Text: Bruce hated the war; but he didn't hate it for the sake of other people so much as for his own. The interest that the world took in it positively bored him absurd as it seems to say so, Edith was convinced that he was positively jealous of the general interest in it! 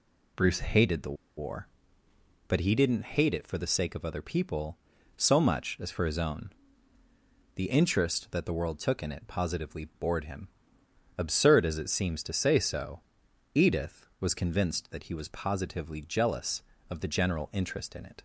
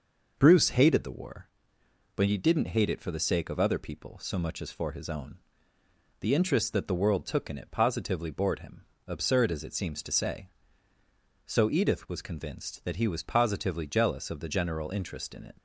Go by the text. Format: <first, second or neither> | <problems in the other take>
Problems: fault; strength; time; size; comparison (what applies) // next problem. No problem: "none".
second | pauses between "the" and "war"; slight; at 1.1 s; 0.22 s long // pauses between "him" and "absurd"; noticeable; at 10.4 s; 0.70 s long; slight in the second